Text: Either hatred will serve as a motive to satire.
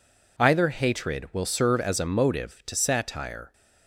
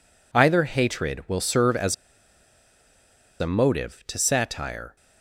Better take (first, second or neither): first